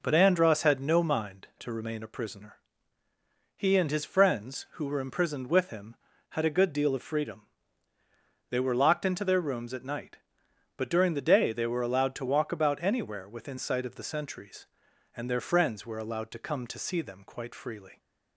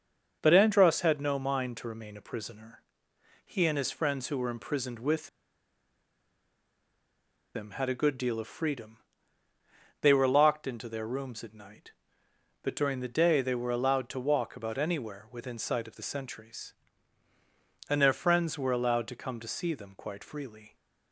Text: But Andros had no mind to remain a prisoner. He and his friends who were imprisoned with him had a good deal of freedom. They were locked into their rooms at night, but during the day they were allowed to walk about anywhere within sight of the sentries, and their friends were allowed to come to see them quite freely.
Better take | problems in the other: first | starts louder than the rest; until 1.4 s; 6.5 dB // pauses between "with" and "him"; strong; at 5.2 s; 2.2 s long

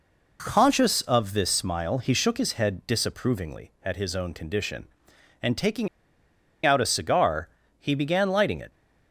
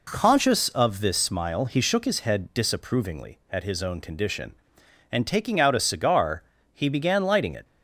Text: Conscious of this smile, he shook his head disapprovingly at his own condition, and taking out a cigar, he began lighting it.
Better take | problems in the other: second | pauses between "taking" and "out"; noticeable; at 5.8 s; 0.78 s long

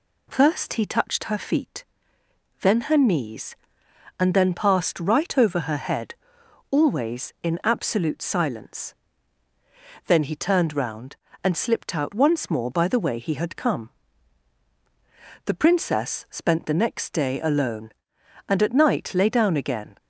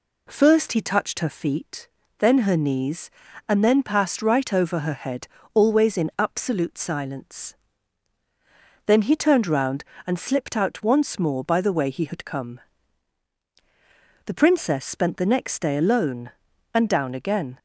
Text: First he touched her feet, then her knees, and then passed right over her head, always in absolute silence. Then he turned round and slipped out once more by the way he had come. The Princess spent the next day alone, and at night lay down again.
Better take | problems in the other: first | skips "at night lay"; at 16.8 s

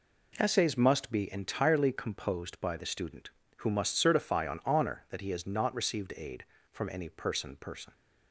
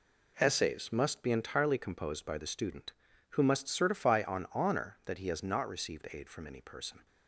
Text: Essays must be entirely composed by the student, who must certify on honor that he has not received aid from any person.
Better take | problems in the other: second | says "person" twice; at 7.5 s

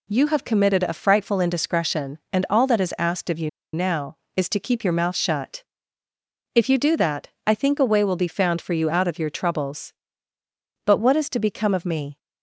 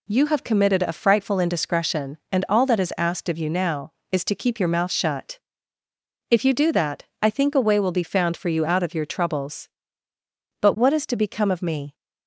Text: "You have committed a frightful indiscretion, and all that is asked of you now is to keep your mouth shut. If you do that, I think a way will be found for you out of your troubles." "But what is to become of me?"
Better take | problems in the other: second | pauses between "you" and "now"; slight; at 3.4 s; 0.24 s long

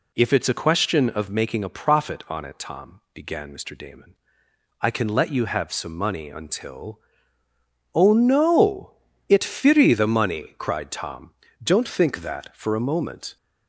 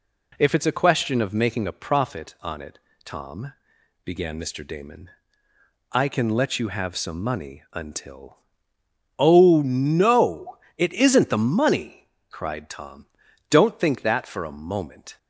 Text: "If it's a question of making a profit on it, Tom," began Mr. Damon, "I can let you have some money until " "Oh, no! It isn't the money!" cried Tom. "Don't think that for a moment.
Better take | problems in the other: second | says "firi" for "isn't"; at 9.4 s

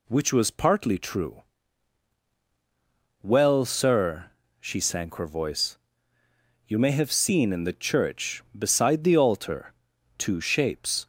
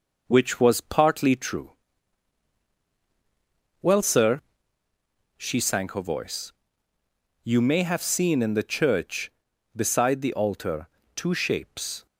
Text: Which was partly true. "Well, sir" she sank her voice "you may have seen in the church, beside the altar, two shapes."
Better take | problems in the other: first | gets quieter; slight; throughout; 3.5 dB // pauses between "sir" and "she"; noticeable; at 4.3 s; 0.96 s long; slight in the first // pauses between "voice" and "you"; noticeable; at 6.5 s; 0.90 s long; noticeable in the first

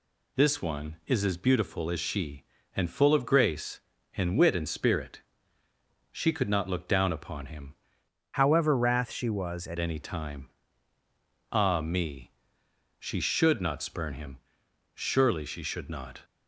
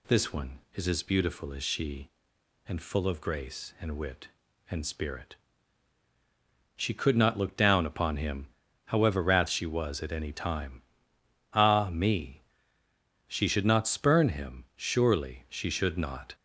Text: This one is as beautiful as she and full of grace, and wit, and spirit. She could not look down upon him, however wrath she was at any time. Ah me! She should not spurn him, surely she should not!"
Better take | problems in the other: second | changes voice from "however" to "at"; from 8.3 to 9.7 s; 1.4 s long

